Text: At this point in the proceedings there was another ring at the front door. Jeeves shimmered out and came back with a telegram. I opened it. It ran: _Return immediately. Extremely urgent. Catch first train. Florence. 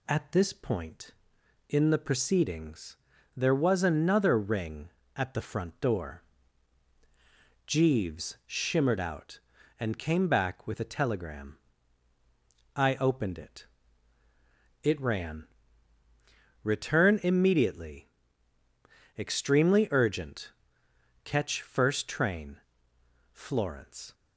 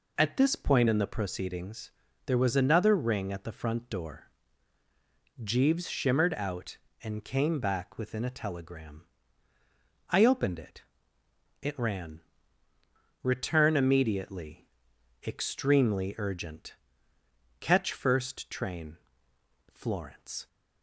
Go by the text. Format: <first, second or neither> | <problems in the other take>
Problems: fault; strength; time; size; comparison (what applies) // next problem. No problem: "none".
first | pauses between "proceedings" and "there"; slight; at 1.9 s; 0.34 s long; also in the first // says "within" for "with"; at 7.9 s